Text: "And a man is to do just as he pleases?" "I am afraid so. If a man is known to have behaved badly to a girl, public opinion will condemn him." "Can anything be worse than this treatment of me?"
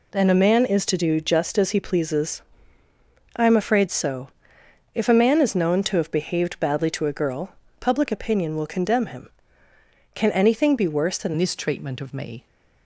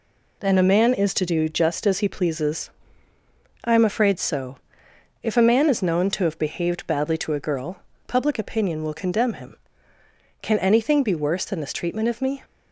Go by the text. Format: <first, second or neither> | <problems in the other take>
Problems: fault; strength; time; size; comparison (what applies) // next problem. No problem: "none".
second | changes voice at "this"; from 11.3 s on; 1.1 s long